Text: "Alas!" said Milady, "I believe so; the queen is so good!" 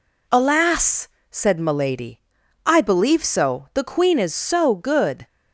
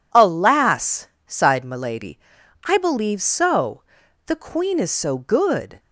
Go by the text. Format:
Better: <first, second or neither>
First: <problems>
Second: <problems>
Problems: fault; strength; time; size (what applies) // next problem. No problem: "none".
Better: first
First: none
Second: says "sighed" for "said"; at 1.2 s